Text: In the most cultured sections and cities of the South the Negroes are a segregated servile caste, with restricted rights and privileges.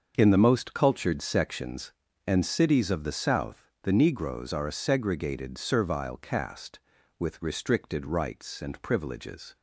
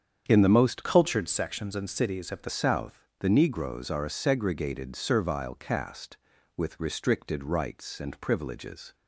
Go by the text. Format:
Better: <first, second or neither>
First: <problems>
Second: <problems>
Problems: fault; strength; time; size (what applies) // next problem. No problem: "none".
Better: first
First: starts louder than the rest; until 1.1 s; 6.5 dB // pauses between "South" and "the"; slight; at 3.6 s; 0.18 s long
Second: starts louder than the rest; strong; until 1.3 s; 8 dB // changes voice from "cultured" to "the"; from 0.8 to 2.4 s; 1.6 s long // pauses between "South" and "the"; slight; at 3.0 s; 0.18 s long